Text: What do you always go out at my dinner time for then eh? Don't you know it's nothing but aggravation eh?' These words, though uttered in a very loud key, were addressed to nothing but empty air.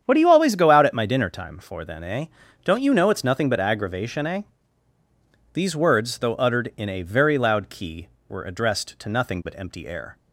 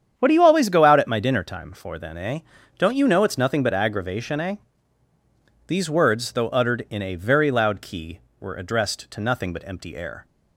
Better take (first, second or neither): neither